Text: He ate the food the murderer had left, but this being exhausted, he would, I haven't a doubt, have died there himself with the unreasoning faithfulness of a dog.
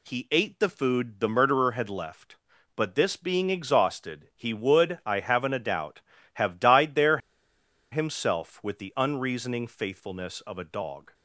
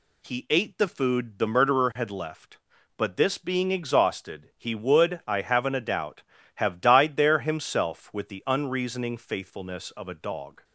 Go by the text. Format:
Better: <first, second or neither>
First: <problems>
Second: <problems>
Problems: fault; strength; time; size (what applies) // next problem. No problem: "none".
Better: second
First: pauses between "there" and "himself"; noticeable; at 7.1 s; 0.73 s long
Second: none